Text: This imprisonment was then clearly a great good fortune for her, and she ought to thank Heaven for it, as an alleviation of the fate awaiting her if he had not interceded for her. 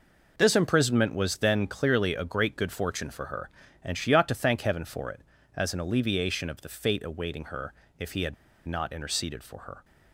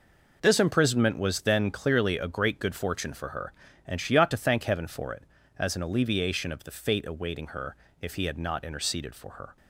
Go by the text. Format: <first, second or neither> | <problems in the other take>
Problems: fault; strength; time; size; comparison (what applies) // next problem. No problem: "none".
second | pauses between "her" and "if"; slight; at 7.7 s; 0.26 s long; slight in the second // pauses between "had" and "not"; slight; at 8.3 s; 0.31 s long